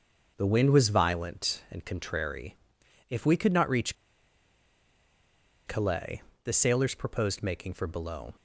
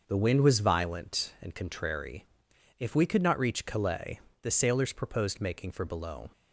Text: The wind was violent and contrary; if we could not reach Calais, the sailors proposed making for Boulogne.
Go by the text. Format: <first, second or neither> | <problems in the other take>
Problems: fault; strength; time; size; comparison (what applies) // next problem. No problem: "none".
second | starts louder than the rest; until 1.3 s; 6 dB; also in the second // pauses between "reach" and "Calais"; strong; at 3.9 s; 1.7 s long